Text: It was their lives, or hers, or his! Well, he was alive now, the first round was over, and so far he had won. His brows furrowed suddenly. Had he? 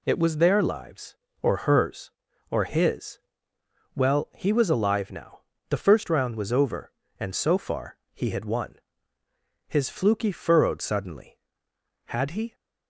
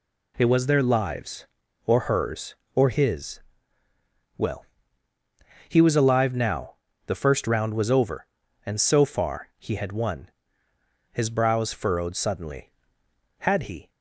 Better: second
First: pauses between "far" and "he"; slight; at 7.9 s; 0.15 s long // says "fluky" for "brows"; at 9.8 s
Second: none

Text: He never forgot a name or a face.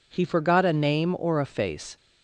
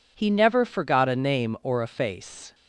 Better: second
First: skips "never"; at 0.2 s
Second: none

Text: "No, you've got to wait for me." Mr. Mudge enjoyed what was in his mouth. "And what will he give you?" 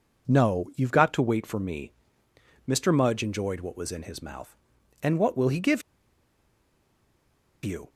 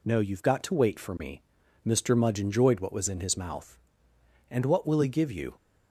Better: second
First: pauses between "give" and "you"; strong; at 5.8 s; 1.8 s long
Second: none

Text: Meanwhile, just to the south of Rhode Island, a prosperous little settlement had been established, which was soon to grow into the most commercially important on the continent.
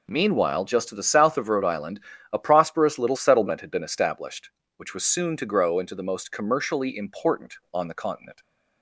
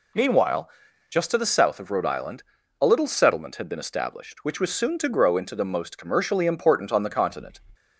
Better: first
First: none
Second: skips "prosperous"; at 2.8 s

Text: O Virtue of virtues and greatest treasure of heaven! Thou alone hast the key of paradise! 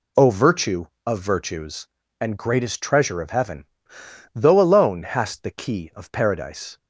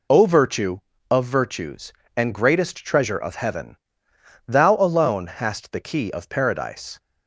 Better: second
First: says "Though" for "Thou"; at 4.3 s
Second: none

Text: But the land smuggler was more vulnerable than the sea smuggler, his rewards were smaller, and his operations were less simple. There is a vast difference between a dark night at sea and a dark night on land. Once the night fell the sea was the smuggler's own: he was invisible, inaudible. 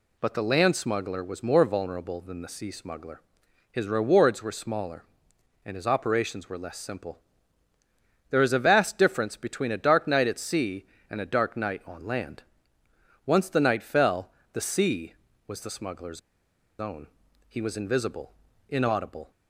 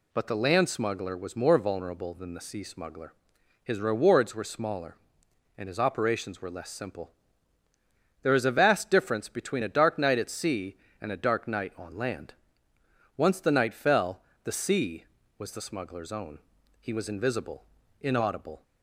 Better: second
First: pauses between "fell" and "the"; slight; at 14.2 s; 0.24 s long // pauses between "smuggler's" and "own"; noticeable; at 16.1 s; 0.59 s long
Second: pauses between "fell" and "the"; slight; at 14.2 s; 0.24 s long

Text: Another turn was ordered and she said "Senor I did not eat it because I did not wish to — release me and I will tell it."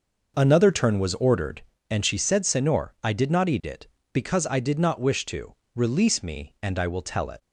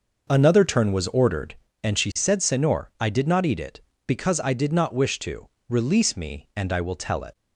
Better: neither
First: none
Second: none

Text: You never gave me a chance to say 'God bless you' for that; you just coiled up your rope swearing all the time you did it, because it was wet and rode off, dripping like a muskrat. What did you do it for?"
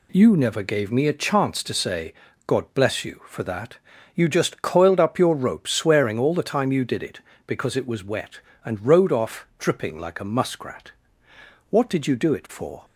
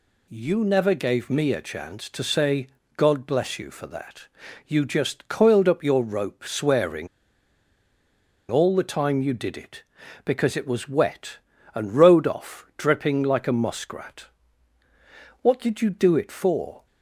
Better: first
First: pauses between "say" and "God"; slight; at 2.1 s; 0.34 s long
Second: pauses between "say" and "God"; slight; at 2.6 s; 0.30 s long // pauses between "swearing" and "all"; strong; at 7.0 s; 1.4 s long

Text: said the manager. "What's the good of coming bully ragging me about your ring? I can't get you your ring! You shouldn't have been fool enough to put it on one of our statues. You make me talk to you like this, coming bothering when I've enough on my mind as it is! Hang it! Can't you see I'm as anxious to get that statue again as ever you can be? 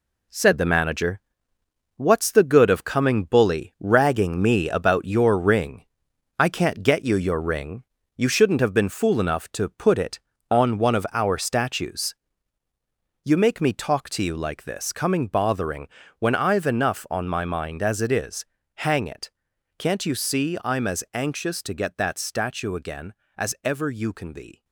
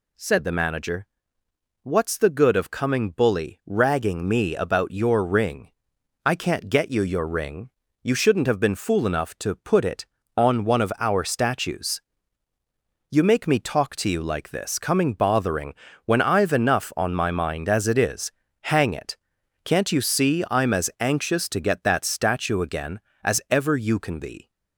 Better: second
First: gets quieter; throughout; 6.5 dB // pauses between "bothering" and "when"; slight; at 15.8 s; 0.30 s long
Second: pauses between "bothering" and "when"; slight; at 15.7 s; 0.30 s long

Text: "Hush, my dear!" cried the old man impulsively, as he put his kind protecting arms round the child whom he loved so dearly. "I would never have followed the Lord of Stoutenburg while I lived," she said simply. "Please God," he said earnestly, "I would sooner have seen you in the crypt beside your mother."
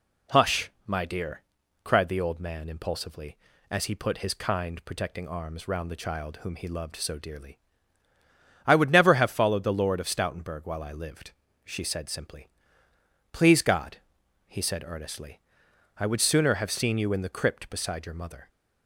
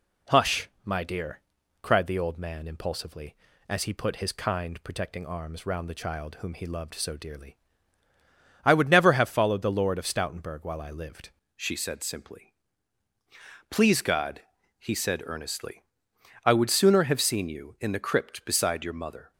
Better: first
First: none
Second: changes voice at "she"; from 11.5 s on; 7.8 s long

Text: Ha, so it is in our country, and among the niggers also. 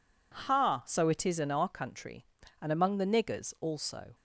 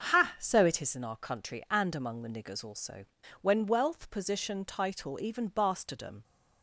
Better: first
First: none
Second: starts louder than the rest; until 1.1 s; 7 dB // goes on to say "When wealth position title even bastardom"; strong; from 3.4 s on; 2.8 s long

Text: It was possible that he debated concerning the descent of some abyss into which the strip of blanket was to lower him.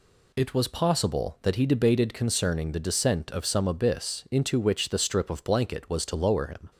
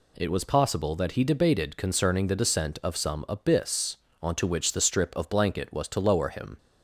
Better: first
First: none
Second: says "onto" for "into"; at 4.2 s

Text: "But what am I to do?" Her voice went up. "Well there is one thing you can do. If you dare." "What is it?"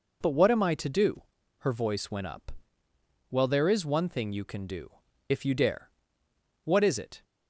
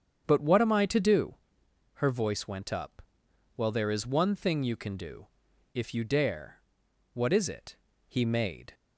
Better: first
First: none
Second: starts louder than the rest; strong; until 1.2 s; 7.5 dB // goes on to say "He made"; noticeable; from 8.0 s on; 0.66 s long

